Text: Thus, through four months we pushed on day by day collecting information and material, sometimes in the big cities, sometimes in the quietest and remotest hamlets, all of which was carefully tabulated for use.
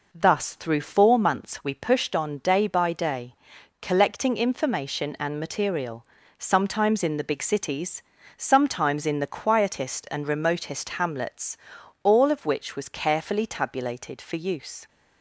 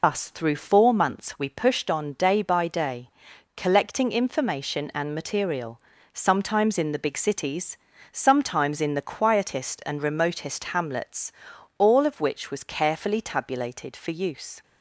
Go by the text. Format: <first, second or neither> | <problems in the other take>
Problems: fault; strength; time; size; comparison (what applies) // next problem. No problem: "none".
first | loses the start of "Thus"; at 0.0 s; 150 ms // pauses between "day" and "collecting"; at 3.1 s; 0.44 s long; also in the first